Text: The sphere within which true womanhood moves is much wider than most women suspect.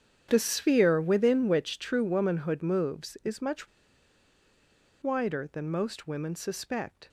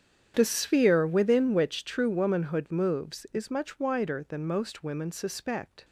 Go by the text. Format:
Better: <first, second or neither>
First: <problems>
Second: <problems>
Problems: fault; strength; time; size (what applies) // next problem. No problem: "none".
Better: second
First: starts louder than the rest; strong; until 1.3 s; 8.5 dB // pauses between "much" and "wider"; strong; at 3.6 s; 1.3 s long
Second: starts louder than the rest; strong; until 1.3 s; 8.5 dB